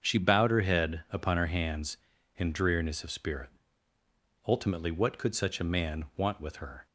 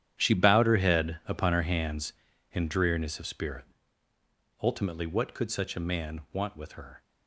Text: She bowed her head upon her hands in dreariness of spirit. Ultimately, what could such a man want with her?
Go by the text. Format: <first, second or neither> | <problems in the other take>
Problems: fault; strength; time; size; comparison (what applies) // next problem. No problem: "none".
first | gets quieter; strong; throughout; 14 dB // starts louder than the rest; strong; until 1.1 s; 10 dB; also in the first